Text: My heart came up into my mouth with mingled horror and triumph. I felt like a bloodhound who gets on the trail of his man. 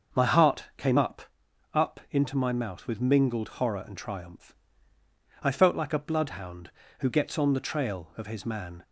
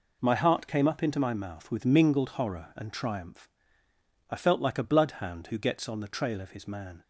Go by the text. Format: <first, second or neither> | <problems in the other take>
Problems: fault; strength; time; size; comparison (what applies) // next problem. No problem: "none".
second | starts louder than the rest; until 1.7 s; 6.5 dB // says "up" twice; at 1.7 s